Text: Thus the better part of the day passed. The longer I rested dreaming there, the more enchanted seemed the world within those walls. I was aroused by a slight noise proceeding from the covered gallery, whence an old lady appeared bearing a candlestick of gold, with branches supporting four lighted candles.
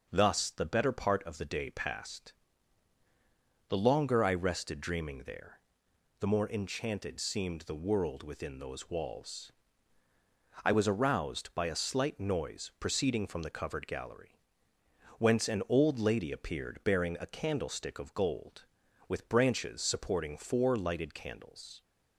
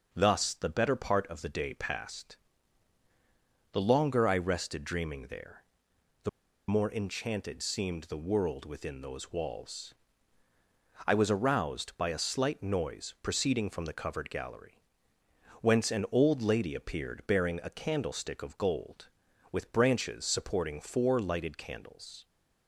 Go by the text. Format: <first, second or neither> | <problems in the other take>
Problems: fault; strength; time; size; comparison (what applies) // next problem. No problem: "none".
first | pauses between "the" and "more"; at 6.2 s; 0.40 s long